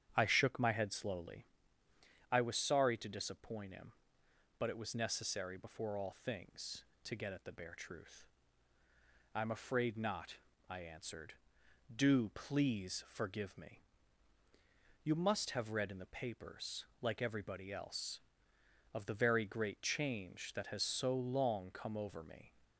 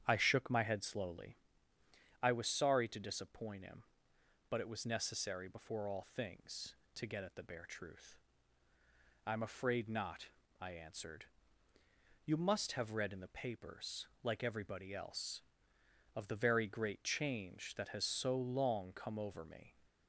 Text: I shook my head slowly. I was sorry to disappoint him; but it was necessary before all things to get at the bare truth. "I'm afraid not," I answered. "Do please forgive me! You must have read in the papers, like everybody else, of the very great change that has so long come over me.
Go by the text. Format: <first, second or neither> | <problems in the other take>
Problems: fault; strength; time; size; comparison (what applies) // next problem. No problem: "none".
first | starts louder than the rest; strong; until 1.0 s; 9.5 dB; strong in the first // skips "Do please forgive me"; at 11.7 s